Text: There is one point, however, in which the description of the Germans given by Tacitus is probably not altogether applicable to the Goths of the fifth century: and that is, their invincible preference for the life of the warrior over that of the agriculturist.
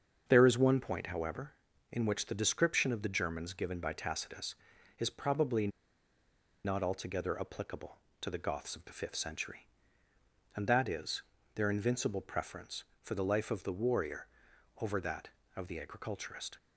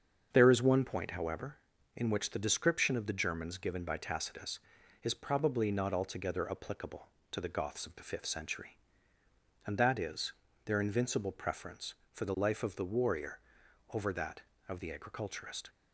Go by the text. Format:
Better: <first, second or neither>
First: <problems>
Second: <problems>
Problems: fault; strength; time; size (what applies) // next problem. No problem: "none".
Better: second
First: starts louder than the rest; until 1.2 s; 7 dB // pauses between "probably" and "not"; noticeable; at 5.6 s; 0.96 s long // pauses between "warrior" and "over"; noticeable; at 14.2 s; 0.52 s long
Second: starts louder than the rest; until 1.3 s; 7 dB // pauses between "warrior" and "over"; noticeable; at 13.4 s; 0.52 s long